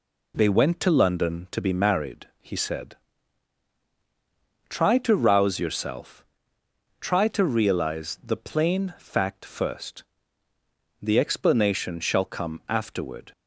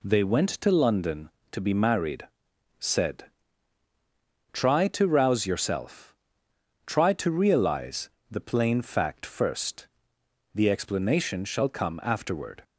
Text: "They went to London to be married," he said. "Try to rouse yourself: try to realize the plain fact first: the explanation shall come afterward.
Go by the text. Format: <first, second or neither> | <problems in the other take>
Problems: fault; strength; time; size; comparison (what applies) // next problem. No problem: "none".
first | skips "he"; at 2.5 s // pauses between "realize" and "the"; slight; at 8.0 s; 0.22 s long